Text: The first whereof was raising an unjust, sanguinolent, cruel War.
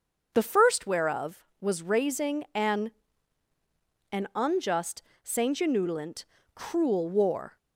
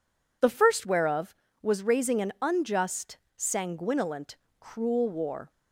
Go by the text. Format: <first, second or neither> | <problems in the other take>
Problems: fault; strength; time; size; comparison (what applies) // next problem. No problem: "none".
second | starts louder than the rest; until 1.3 s; 6.5 dB // says "an" twice; at 4.1 s